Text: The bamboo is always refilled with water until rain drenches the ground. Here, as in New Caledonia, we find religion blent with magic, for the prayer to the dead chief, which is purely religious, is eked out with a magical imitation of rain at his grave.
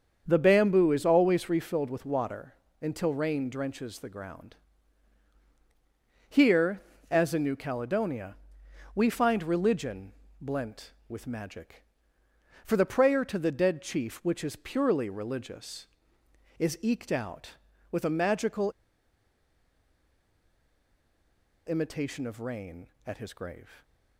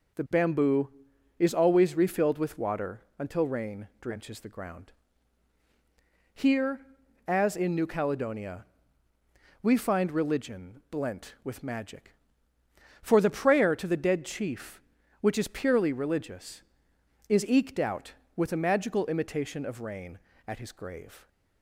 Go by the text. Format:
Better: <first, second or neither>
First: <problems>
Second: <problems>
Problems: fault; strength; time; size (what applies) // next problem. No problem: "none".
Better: second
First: starts louder than the rest; strong; until 1.2 s; 7 dB // pauses between "water" and "until"; slight; at 2.5 s; 0.26 s long // pauses between "religion" and "blent"; slight; at 10.1 s; 0.28 s long // pauses between "magical" and "imitation"; strong; at 18.7 s; 2.9 s long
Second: pauses between "water" and "until"; slight; at 3.0 s; 0.16 s long